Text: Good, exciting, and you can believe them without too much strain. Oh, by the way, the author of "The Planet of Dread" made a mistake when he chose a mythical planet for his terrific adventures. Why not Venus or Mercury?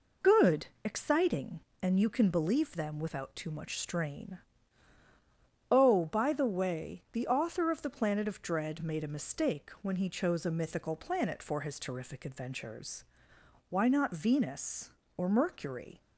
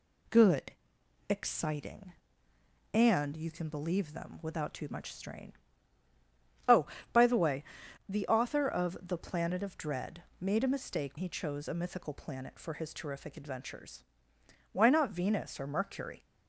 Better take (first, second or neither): first